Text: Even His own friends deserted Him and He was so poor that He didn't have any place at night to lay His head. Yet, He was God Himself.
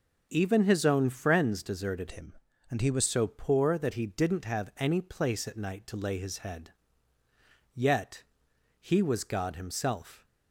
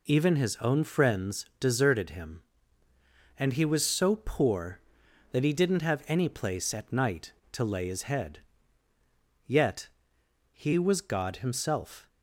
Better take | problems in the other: second | changes voice from "Him" to "was"; from 2.1 to 3.0 s; 0.9 s long

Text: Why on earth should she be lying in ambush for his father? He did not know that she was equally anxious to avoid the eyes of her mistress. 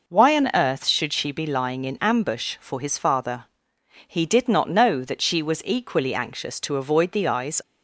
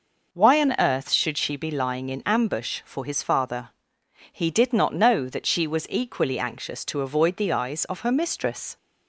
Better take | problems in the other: second | stops before "of her mistress"; at 7.6 s

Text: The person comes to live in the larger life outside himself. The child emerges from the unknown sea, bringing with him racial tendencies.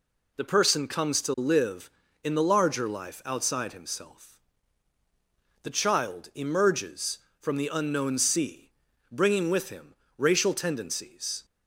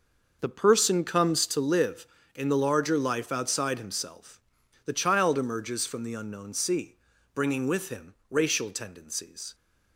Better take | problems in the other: first | starts louder than the rest; noticeable; until 1.6 s; 6 dB // pauses between "him" and "racial"; slight; at 8.1 s; 0.17 s long; slight in the first

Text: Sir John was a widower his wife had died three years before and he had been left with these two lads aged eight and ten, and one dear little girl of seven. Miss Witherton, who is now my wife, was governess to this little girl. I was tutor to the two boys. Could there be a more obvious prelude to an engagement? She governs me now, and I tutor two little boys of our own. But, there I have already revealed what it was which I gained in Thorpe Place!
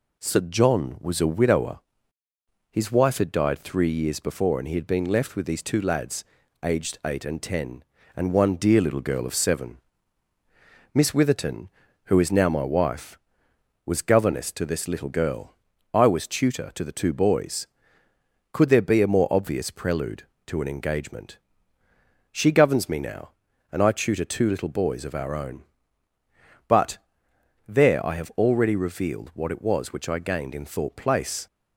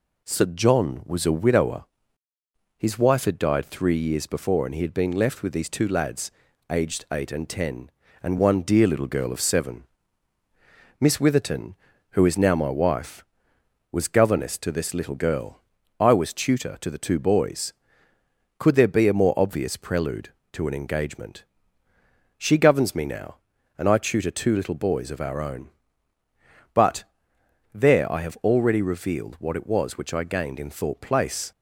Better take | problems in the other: neither | pauses between "widower" and "his"; noticeable; the same in both // pauses between "lads" and "aged"; the same in both

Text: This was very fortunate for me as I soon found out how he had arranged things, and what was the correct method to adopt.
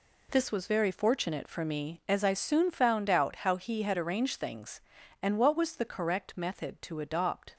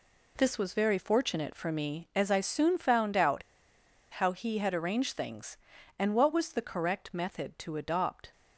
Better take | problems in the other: first | pauses between "out" and "how"; noticeable; at 3.4 s; 0.70 s long

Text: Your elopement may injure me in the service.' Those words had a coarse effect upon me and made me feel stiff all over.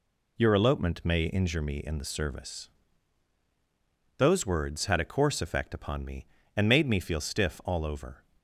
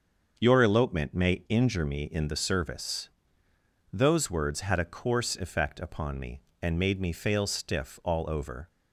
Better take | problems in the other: first | starts louder than the rest; until 1.3 s; 6.5 dB // says "fail" for "feel"; at 7.1 s

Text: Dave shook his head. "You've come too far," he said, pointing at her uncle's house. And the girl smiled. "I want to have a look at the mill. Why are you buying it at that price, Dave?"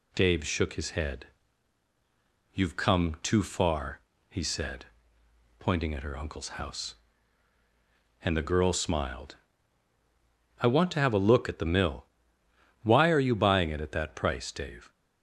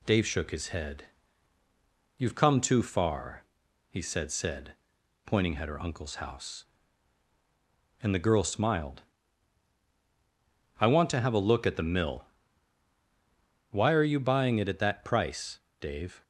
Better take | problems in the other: first | says "said" twice; at 4.3 s

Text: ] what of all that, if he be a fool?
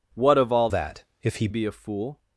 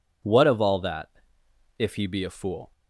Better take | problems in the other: second | changes voice from "that" to "he"; from 0.6 to 1.4 s; 0.8 s long

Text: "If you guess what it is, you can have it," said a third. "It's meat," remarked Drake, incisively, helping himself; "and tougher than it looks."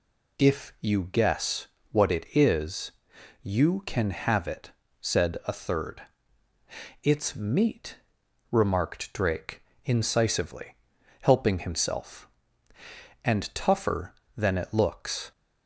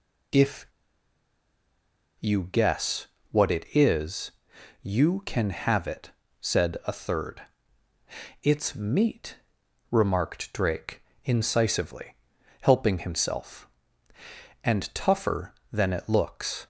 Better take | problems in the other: first | pauses between "If" and "you"; strong; at 0.6 s; 1.5 s long // pauses between "guess" and "what"; slight; at 3.0 s; 0.26 s long; slight in the first

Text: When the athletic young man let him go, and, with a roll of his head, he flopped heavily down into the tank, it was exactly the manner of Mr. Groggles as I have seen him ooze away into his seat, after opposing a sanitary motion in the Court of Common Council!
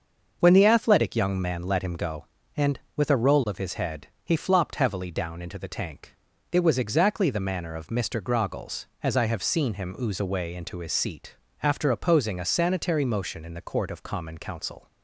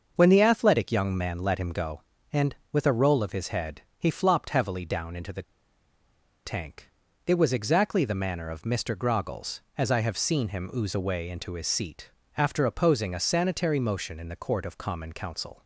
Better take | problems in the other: first | starts louder than the rest; until 1.1 s; 6.5 dB; also in the first // pauses between "the" and "tank"; at 5.4 s; 1.0 s long

